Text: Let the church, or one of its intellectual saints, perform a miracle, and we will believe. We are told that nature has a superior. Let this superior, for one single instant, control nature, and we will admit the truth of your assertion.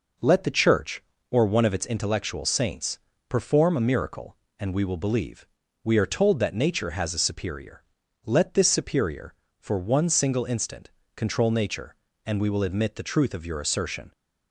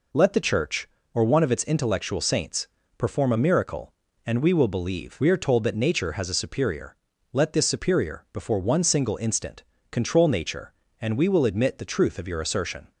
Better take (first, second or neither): first